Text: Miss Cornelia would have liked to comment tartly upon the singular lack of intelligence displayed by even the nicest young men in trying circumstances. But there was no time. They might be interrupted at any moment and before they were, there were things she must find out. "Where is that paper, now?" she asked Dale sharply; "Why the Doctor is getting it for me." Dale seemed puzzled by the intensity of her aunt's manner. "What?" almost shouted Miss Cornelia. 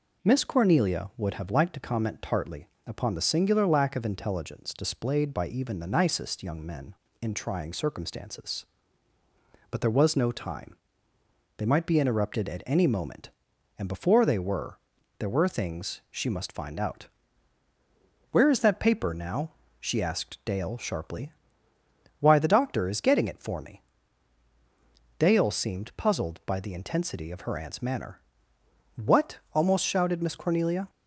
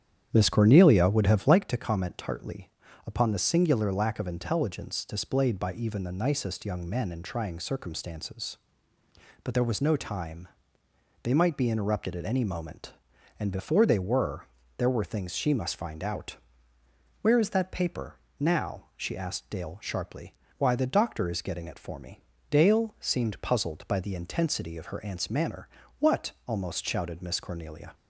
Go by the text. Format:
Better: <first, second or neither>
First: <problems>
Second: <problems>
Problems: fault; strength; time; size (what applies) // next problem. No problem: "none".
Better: first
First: pauses between "tartly" and "upon"; slight; at 2.6 s; 0.18 s long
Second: starts louder than the rest; strong; until 1.6 s; 9.5 dB // pauses between "tartly" and "upon"; slight; at 2.6 s; 0.36 s long